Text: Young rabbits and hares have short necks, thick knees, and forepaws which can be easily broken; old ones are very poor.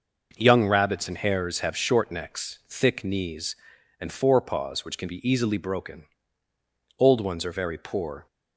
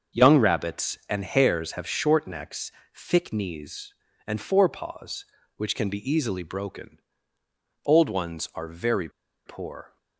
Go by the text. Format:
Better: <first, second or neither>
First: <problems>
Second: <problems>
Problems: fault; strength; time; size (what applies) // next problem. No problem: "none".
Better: first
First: none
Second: starts louder than the rest; until 1.2 s; 6.5 dB // pauses between "very" and "poor"; at 9.0 s; 0.37 s long